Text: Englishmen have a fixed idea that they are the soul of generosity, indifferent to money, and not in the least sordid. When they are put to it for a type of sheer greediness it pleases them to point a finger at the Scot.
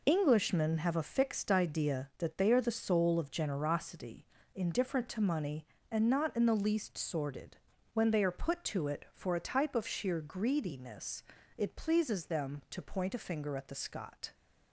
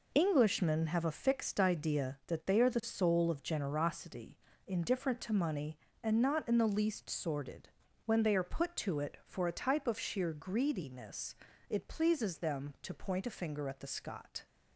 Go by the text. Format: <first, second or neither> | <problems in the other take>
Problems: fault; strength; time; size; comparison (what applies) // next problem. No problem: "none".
neither | pauses between "greediness" and "it"; slight; the same in both